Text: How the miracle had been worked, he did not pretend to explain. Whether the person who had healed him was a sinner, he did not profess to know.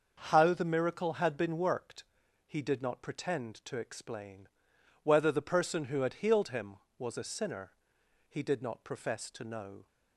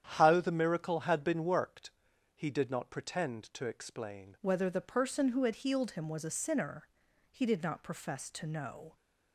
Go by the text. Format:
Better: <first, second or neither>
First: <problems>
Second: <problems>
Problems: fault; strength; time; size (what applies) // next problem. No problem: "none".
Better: first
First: starts louder than the rest; until 1.2 s; 6 dB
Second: starts louder than the rest; strong; until 1.0 s; 9 dB // changes voice at "Whether"; from 4.4 s on; 4.5 s long